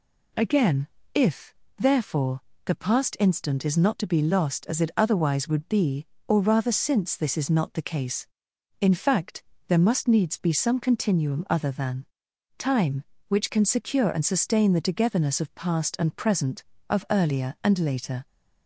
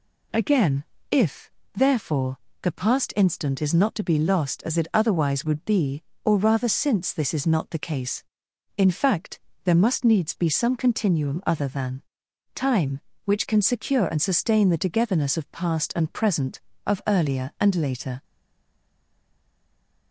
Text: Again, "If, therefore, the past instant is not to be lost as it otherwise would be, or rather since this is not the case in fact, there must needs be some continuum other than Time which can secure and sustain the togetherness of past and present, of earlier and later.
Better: first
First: pauses between "than" and "Time"; noticeable; at 12.0 s; 0.54 s long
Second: pauses between "than" and "Time"; noticeable; at 12.0 s; 0.54 s long // stays silent after the last word; noticeable; from 18.2 s on; 1.9 s long

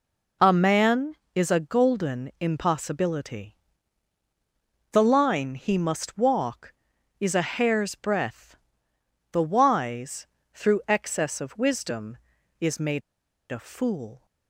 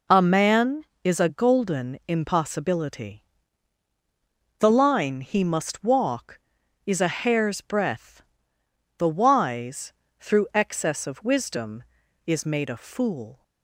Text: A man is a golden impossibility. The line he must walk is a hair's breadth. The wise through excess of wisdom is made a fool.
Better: second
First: pauses between "wise" and "through"; slight; at 10.2 s; 0.26 s long // pauses between "made" and "a"; noticeable; at 13.0 s; 0.49 s long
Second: pauses between "wise" and "through"; slight; at 9.9 s; 0.26 s long

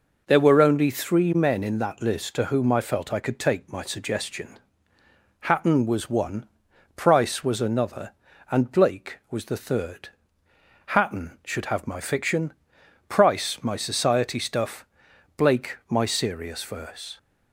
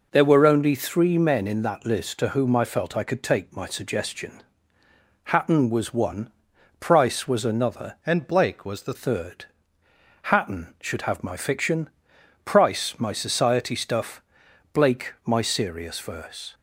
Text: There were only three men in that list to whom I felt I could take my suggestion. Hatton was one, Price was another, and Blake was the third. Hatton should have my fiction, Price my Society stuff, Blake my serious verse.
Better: first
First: none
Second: changes voice from "and" to "the"; from 8.0 to 8.9 s; 0.9 s long

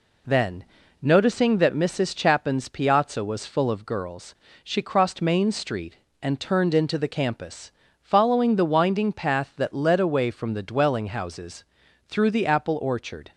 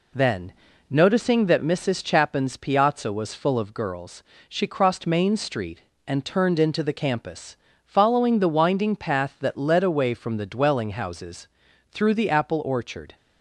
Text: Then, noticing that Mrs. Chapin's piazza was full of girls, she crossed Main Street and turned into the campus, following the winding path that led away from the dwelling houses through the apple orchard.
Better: neither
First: pauses between "houses" and "through"; at 11.6 s; 0.44 s long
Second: pauses between "houses" and "through"; at 11.4 s; 0.44 s long

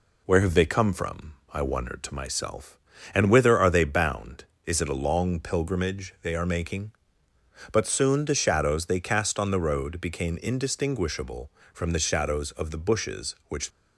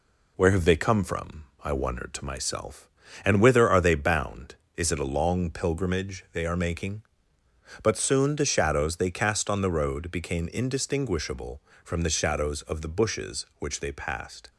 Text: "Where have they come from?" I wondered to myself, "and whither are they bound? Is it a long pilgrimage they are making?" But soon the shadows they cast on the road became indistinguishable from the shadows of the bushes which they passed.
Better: second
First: stops before "they passed"; at 13.6 s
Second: none

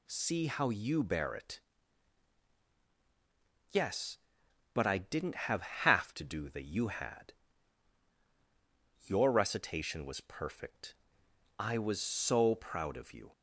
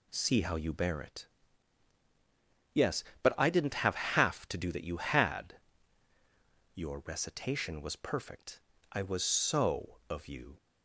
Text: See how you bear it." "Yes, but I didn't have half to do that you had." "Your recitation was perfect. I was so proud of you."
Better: first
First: none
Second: skips "proud"; at 10.0 s

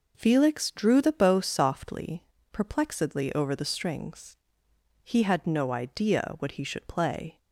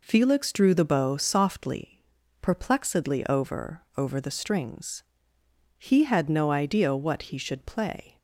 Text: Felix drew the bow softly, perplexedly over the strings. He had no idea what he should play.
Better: first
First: none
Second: says "over" twice; at 3.9 s

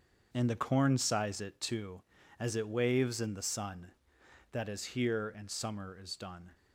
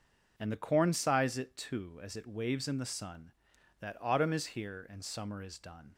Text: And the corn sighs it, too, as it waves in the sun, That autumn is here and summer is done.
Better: second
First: starts louder than the rest; until 1.3 s; 6.5 dB // skips "autumn"; at 4.6 s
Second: none

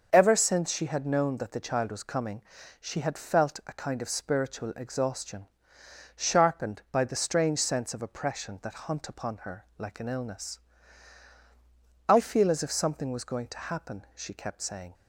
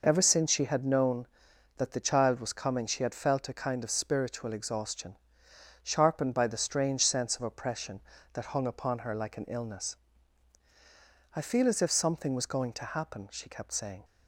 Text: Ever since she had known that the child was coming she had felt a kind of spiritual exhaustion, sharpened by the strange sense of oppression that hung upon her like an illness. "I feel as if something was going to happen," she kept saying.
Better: second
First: starts louder than the rest; noticeable; until 1.1 s; 6 dB // pauses between "coming" and "she"; at 2.4 s; 0.38 s long // says "hunt" for "hung"; at 8.8 s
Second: none

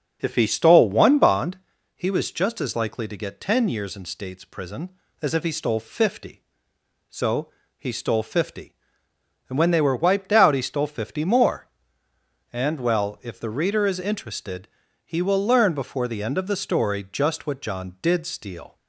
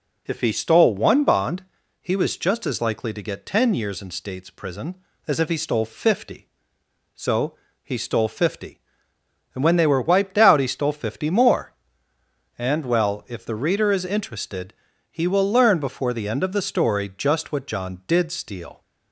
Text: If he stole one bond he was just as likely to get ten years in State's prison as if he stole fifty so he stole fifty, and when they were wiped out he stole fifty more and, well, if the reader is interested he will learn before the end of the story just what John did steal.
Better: second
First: starts louder than the rest; noticeable; until 1.5 s; 6 dB // pauses between "bond" and "he"; at 1.5 s; 0.38 s long // pauses between "so" and "he"; slight; at 7.4 s; 0.30 s long // pauses between "interested" and "he"; at 14.6 s; 0.38 s long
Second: pauses between "bond" and "he"; at 1.6 s; 0.38 s long // pauses between "so" and "he"; slight; at 7.5 s; 0.30 s long // pauses between "interested" and "he"; at 14.7 s; 0.38 s long

